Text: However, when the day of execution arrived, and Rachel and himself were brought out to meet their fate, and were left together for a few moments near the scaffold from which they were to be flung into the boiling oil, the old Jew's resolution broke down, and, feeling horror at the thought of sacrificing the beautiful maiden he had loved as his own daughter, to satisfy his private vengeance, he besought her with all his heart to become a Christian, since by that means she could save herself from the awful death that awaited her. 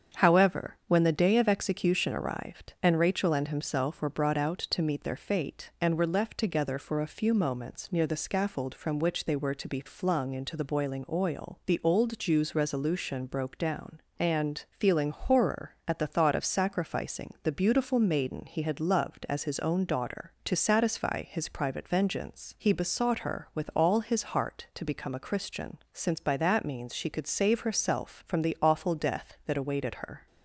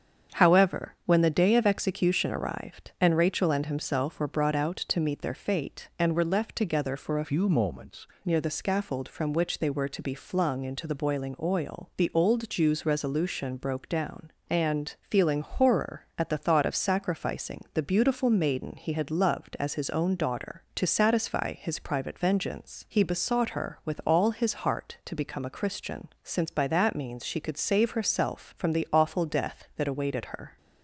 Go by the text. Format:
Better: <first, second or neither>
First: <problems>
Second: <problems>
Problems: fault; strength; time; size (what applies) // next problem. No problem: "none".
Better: first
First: starts louder than the rest; strong; until 1.2 s; 7.5 dB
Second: starts louder than the rest; strong; until 1.4 s; 7.5 dB // changes voice from "few" to "moments"; from 7.2 to 8.0 s; 0.8 s long